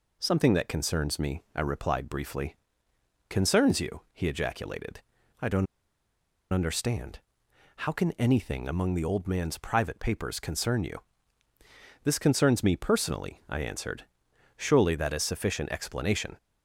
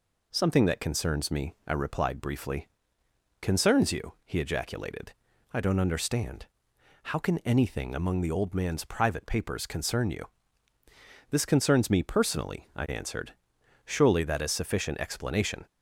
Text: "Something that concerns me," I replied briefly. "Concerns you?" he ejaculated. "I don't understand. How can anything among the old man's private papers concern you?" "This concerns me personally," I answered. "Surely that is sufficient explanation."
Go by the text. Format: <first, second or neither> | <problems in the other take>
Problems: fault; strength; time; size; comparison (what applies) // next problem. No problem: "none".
second | pauses between "don't" and "understand"; noticeable; at 5.6 s; 0.87 s long